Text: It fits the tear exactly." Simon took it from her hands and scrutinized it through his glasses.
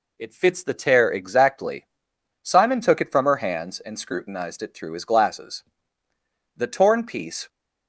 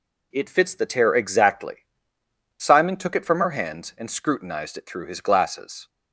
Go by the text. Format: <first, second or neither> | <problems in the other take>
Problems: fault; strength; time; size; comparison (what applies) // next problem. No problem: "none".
second | goes on to say "The torn piece"; noticeable; from 6.5 s on; 0.92 s long